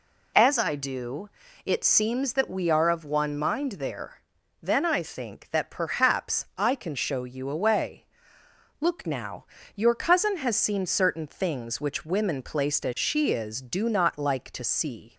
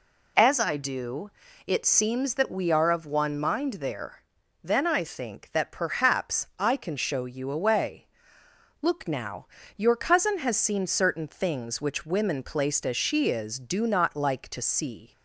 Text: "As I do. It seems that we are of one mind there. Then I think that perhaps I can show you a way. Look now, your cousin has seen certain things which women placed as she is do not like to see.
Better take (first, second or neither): neither